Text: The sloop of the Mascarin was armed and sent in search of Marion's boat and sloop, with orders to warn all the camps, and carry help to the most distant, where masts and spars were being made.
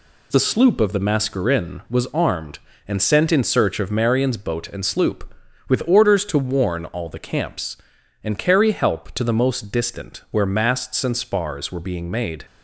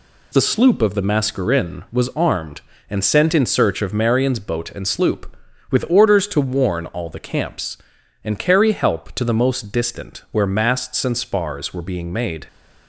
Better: neither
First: none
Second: none

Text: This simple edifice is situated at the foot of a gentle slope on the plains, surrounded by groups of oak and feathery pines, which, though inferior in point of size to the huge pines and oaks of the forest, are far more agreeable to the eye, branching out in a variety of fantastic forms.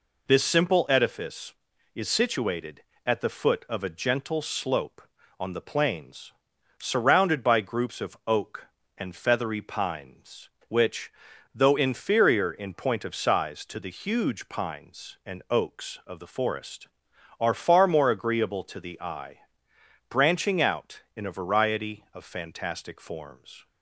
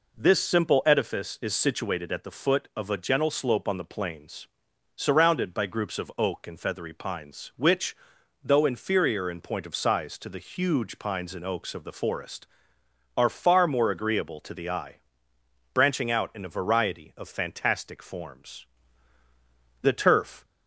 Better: first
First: none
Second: goes on to say "The turf"; noticeable; from 19.8 s on; 0.62 s long

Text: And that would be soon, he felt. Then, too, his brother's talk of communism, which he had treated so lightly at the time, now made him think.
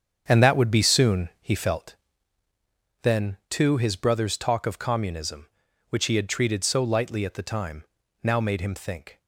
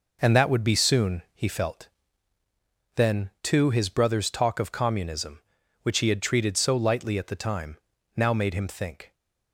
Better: second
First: starts louder than the rest; strong; until 2.1 s; 8 dB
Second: none

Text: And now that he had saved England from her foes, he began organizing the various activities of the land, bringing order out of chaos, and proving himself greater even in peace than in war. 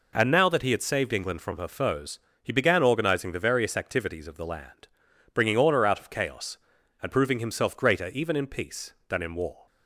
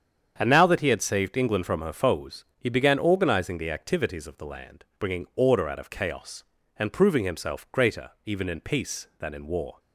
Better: first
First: none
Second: starts louder than the rest; strong; until 1.3 s; 8 dB // skips "various"; at 3.7 s

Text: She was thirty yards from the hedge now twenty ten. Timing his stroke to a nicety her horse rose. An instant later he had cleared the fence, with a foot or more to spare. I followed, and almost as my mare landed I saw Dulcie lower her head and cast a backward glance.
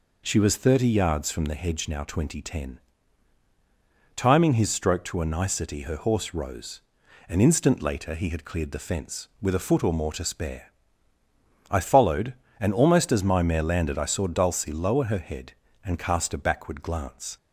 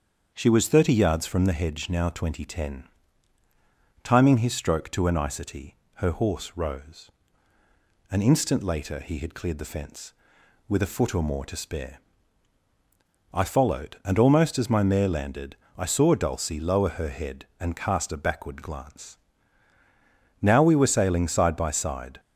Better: first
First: none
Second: starts louder than the rest; until 1.3 s; 7 dB // pauses between "nicety" and "her"; slight; at 5.7 s; 0.22 s long // pauses between "landed" and "I"; slight; at 15.5 s; 0.22 s long // goes on to say "Now we were sailing side by side"; strong; from 20.4 s on; 1.7 s long

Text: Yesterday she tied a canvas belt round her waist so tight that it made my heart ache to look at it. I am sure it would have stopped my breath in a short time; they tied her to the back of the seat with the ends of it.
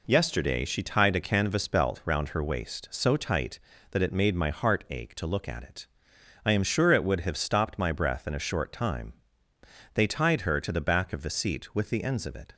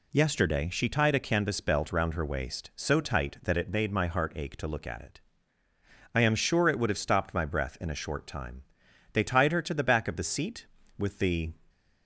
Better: first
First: none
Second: stops before "ends of it"; at 11.6 s

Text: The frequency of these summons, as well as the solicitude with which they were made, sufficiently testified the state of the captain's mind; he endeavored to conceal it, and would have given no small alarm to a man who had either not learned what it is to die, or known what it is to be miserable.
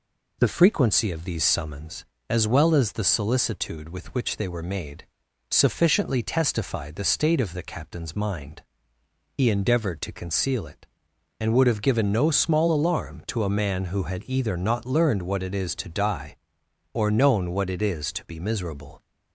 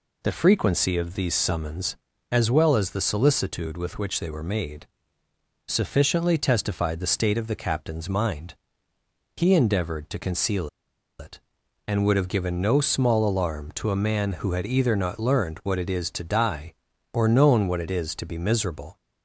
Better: first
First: none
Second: pauses between "conceal" and "it"; noticeable; at 10.6 s; 0.50 s long

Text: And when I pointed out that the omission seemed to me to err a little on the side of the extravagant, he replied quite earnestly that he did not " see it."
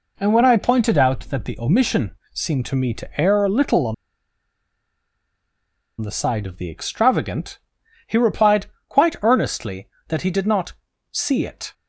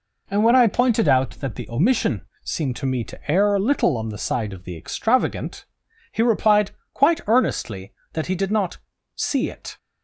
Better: second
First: pauses between "omission" and "seemed"; slight; at 2.1 s; 0.22 s long // pauses between "on" and "the"; strong; at 3.9 s; 2.0 s long // pauses between "replied" and "quite"; slight; at 8.6 s; 0.22 s long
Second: pauses between "omission" and "seemed"; slight; at 2.2 s; 0.22 s long // pauses between "replied" and "quite"; slight; at 6.6 s; 0.22 s long

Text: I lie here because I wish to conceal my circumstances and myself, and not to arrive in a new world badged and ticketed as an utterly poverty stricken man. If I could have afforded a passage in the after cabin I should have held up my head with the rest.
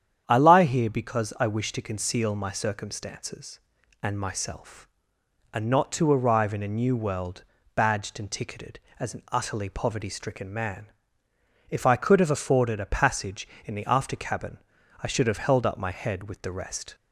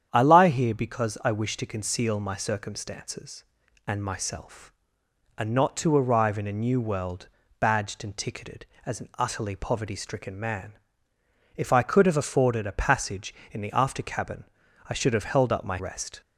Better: first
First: starts louder than the rest; strong; until 1.2 s; 9 dB // pauses between "world" and "badged"; slight; at 7.4 s; 0.32 s long // pauses between "cabin" and "I"; at 14.5 s; 0.42 s long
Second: starts louder than the rest; strong; until 1.1 s; 9 dB // pauses between "world" and "badged"; slight; at 7.2 s; 0.32 s long // pauses between "cabin" and "I"; at 14.4 s; 0.42 s long // skips "head with the"; at 15.7 s

